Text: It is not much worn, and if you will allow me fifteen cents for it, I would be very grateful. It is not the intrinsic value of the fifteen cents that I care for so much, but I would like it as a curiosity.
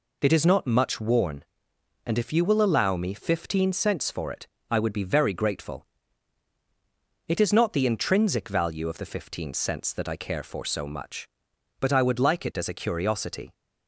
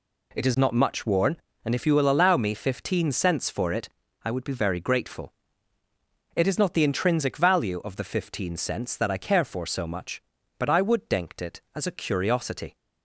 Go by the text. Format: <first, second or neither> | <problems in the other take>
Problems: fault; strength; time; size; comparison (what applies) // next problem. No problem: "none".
first | says "denkt" for "like"; at 11.0 s